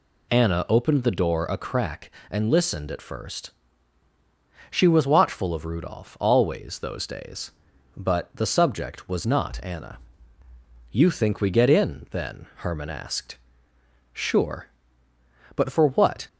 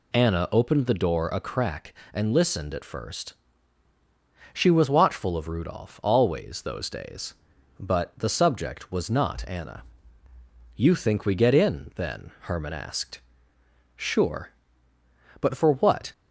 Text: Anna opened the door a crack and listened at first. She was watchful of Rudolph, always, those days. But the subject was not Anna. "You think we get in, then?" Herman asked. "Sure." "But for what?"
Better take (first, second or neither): neither